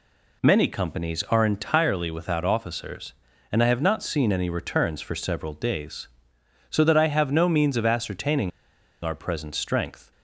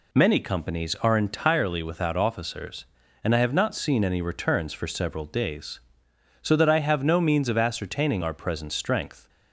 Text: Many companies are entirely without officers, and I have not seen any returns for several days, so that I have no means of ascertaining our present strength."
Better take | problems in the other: second | pauses between "ascertaining" and "our"; noticeable; at 8.5 s; 0.54 s long

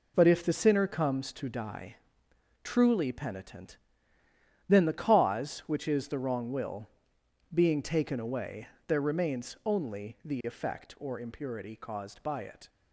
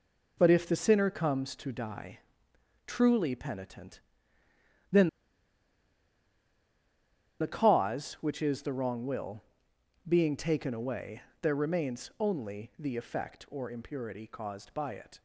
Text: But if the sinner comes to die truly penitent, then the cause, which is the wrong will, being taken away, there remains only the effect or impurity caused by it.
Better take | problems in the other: first | pauses between "die" and "truly"; noticeable; at 2.2 s; 0.66 s long; noticeable in the first // pauses between "then" and "the"; strong; at 5.0 s; 2.3 s long

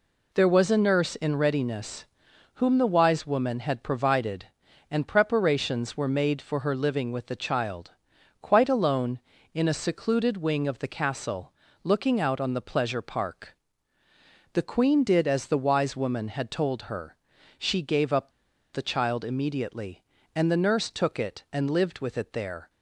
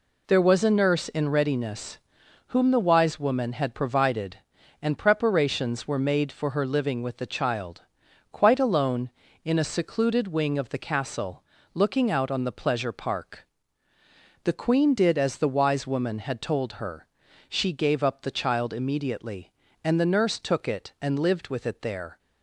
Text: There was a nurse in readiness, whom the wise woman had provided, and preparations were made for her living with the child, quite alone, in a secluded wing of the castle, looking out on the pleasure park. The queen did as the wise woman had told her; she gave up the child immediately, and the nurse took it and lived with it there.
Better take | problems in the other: second | pauses between "up" and "the"; at 18.2 s; 0.43 s long

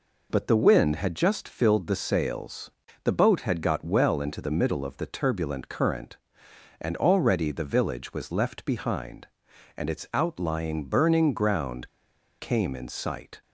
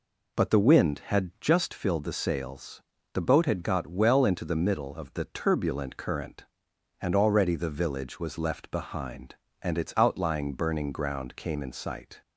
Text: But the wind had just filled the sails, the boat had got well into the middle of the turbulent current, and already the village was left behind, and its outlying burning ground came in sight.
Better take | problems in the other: second | pauses between "ground" and "came"; noticeable; at 11.8 s; 0.50 s long

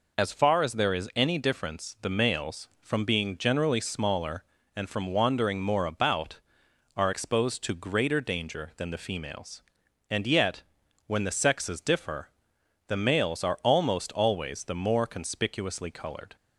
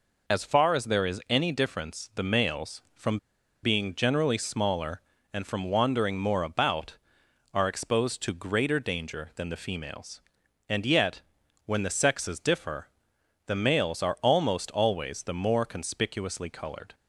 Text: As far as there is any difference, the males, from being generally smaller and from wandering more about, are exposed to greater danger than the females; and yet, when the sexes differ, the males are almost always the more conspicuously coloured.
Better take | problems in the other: first | pauses between "from" and "being"; noticeable; at 3.1 s; 0.46 s long

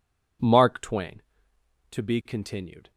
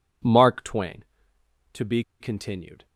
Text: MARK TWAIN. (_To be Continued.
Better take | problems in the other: first | pauses between "be" and "Continued"; slight; at 2.0 s; 0.19 s long

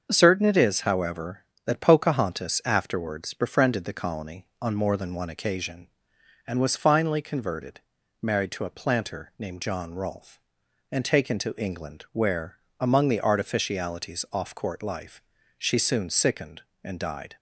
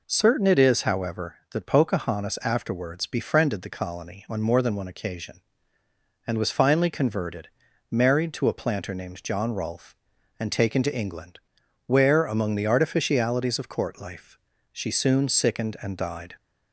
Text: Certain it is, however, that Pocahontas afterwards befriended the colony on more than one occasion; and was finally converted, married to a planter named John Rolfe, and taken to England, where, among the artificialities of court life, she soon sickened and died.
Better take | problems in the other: second | starts louder than the rest; until 1.1 s; 6.5 dB // says "off" for "of"; at 14.3 s

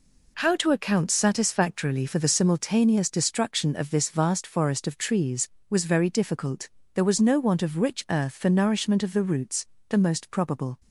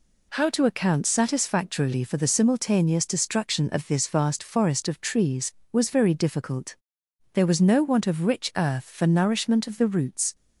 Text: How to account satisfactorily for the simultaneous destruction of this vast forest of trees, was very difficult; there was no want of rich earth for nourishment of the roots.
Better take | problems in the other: second | goes on to say "The most probable"; noticeable; from 9.8 s on; 0.90 s long

